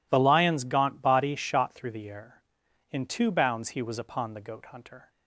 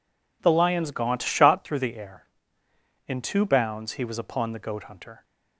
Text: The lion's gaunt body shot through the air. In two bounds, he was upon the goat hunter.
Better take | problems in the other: first | skips "body"; at 1.2 s

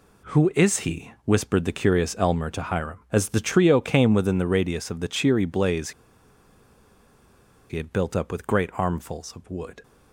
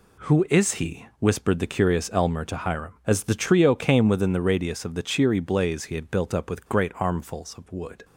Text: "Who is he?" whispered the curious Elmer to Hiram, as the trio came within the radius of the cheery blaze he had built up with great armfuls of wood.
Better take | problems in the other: second | pauses between "blaze" and "he"; strong; at 5.9 s; 1.7 s long

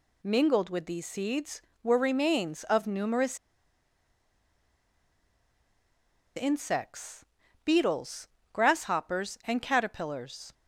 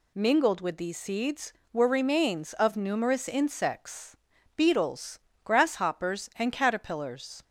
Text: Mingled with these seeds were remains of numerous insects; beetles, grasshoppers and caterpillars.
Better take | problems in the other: second | pauses between "numerous" and "insects"; strong; at 3.3 s; 2.9 s long

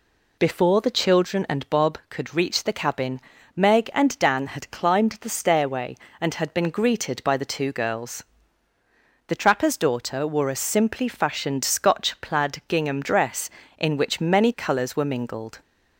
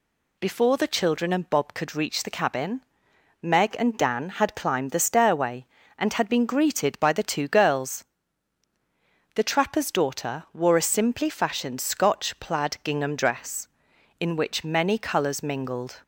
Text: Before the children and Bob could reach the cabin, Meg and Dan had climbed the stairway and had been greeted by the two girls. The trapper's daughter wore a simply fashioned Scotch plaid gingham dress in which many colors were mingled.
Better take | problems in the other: first | skips "were"; at 15.4 s

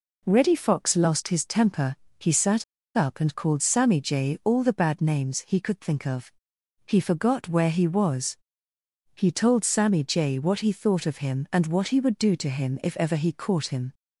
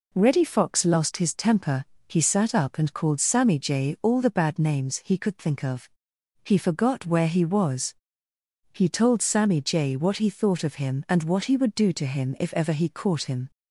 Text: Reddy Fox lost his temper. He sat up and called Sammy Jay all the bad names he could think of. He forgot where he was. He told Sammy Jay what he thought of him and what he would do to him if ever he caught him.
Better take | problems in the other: second | pauses between "sat" and "up"; slight; at 2.6 s; 0.31 s long

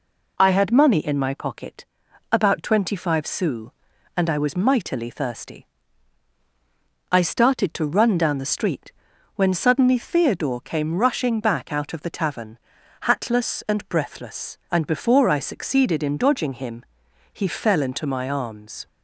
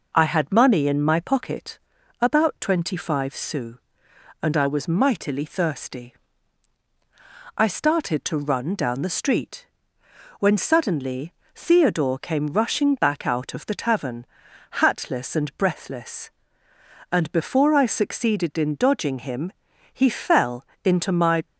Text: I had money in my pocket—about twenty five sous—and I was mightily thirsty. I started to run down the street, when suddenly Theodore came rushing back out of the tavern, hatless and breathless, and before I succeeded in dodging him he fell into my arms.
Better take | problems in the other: first | pauses between "suddenly" and "Theodore"; slight; at 11.3 s; 0.22 s long // pauses between "him" and "he"; at 19.5 s; 0.44 s long; noticeable in the first // pauses between "fell" and "into"; slight; at 20.6 s; 0.22 s long // stops before "arms"; at 21.4 s

